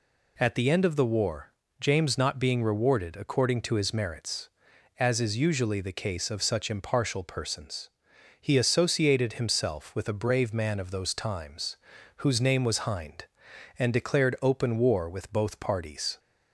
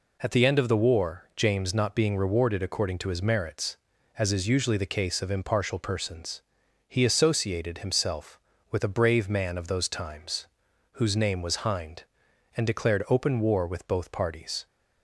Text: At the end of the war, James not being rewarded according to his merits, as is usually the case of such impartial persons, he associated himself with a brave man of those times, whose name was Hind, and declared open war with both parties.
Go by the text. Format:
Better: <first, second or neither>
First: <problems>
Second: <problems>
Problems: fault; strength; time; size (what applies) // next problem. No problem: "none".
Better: first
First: none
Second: skips "such"; at 5.2 s